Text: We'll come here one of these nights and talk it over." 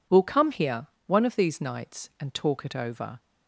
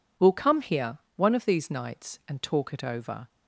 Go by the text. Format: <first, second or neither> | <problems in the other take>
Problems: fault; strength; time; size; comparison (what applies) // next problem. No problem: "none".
neither | pauses between "here" and "one"; slight; the same in both